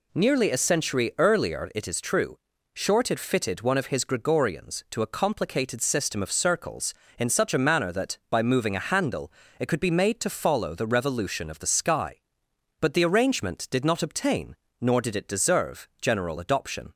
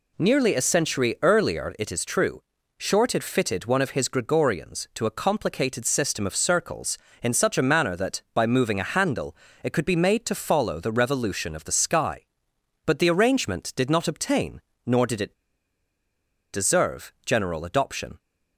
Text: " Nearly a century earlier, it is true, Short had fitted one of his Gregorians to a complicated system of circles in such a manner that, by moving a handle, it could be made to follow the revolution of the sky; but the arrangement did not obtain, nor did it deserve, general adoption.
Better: first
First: none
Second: pauses between "it" and "deserve"; at 15.3 s; 1.1 s long

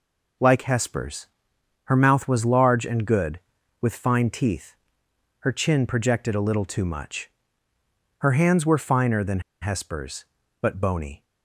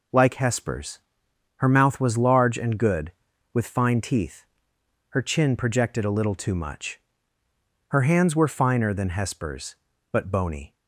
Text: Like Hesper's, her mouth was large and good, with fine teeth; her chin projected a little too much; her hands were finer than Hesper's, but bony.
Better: second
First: pauses between "than" and "Hesper's"; slight; at 9.3 s; 0.21 s long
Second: none

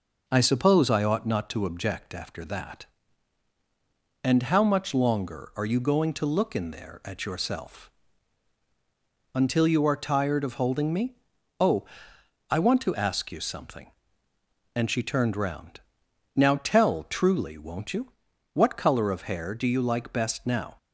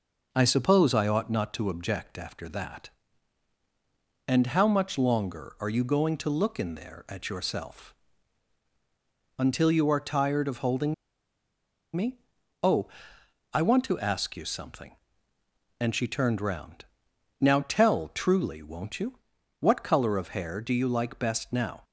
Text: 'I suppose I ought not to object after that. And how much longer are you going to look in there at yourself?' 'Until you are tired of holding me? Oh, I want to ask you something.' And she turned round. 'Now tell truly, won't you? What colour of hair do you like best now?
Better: first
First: none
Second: pauses between "holding" and "me"; at 10.9 s; 1.0 s long

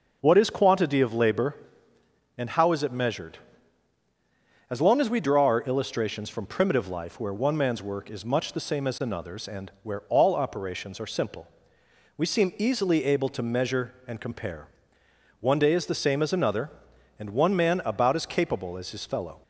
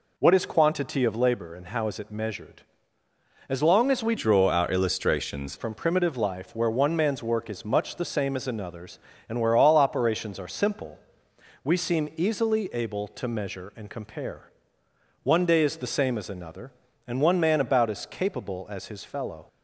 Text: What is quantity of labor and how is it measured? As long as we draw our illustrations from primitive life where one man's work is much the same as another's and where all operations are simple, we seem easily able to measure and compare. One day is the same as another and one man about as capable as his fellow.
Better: first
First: none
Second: changes voice from "draw" to "illustrations"; from 4.1 to 5.5 s; 1.4 s long

